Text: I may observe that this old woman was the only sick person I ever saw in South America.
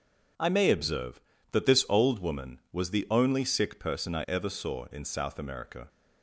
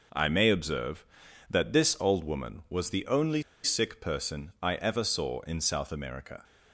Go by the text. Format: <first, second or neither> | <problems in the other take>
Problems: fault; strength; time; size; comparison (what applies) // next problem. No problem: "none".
first | pauses between "only" and "sick"; slight; at 3.4 s; 0.21 s long